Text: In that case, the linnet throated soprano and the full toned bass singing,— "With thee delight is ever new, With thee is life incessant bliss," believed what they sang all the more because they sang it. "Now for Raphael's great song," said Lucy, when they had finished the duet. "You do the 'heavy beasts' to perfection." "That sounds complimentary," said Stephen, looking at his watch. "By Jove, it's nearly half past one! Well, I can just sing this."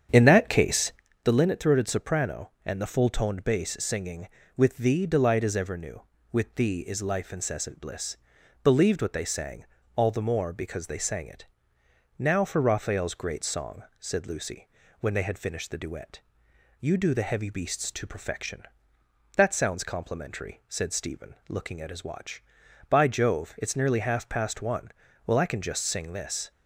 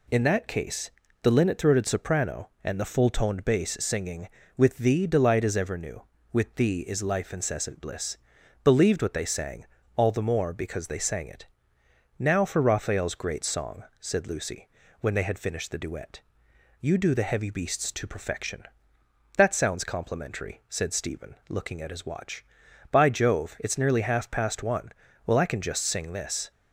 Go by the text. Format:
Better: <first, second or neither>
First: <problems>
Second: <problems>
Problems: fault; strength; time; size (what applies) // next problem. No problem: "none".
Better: second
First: starts louder than the rest; strong; until 1.1 s; 8 dB // pauses between "sang" and "all"; slight; at 9.6 s; 0.30 s long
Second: pauses between "sang" and "all"; slight; at 9.6 s; 0.30 s long